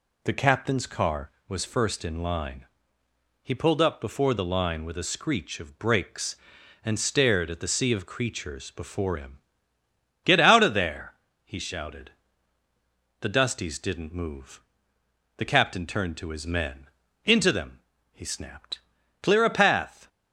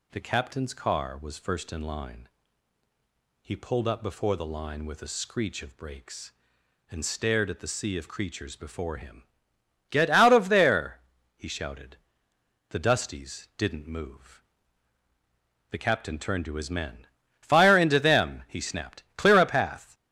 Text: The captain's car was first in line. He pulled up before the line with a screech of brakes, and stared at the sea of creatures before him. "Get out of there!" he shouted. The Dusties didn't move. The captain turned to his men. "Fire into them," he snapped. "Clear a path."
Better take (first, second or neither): second